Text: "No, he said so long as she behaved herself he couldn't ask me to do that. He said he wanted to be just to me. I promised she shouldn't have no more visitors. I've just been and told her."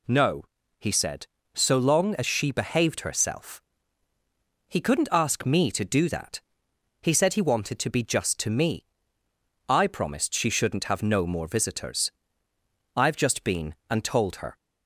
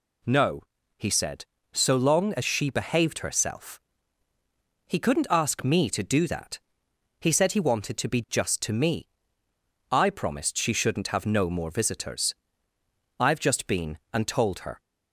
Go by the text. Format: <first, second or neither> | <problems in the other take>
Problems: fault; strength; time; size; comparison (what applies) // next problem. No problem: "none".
neither | pauses between "herself" and "he"; the same in both